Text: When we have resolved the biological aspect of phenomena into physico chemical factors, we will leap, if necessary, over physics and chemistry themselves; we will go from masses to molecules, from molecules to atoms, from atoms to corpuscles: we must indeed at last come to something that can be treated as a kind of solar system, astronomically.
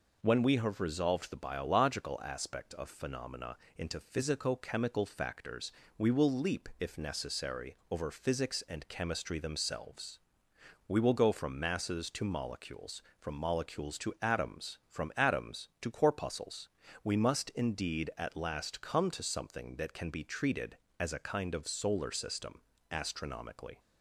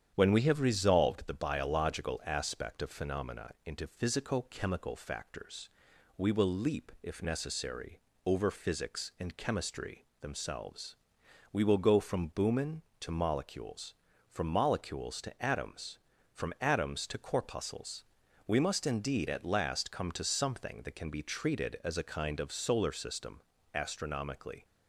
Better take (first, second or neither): first